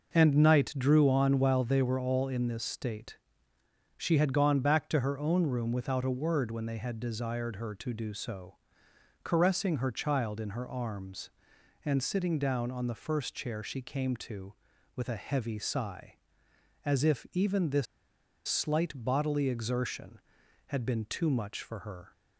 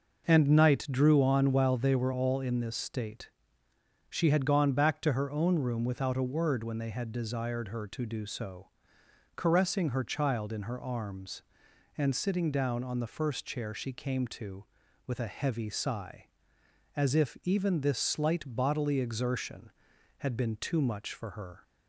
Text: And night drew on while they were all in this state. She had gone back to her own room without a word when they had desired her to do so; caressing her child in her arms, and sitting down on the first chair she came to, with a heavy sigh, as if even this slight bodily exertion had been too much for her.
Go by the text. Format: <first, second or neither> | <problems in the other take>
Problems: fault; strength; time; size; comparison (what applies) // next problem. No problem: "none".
second | pauses between "this" and "slight"; noticeable; at 17.8 s; 0.62 s long